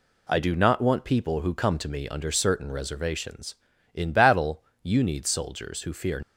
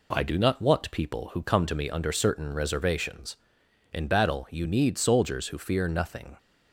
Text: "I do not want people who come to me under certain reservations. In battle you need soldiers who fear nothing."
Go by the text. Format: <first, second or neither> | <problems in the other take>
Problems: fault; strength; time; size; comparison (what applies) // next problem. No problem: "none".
second | pauses between "battle" and "you"; slight; at 4.6 s; 0.20 s long // stops before "nothing"; at 6.2 s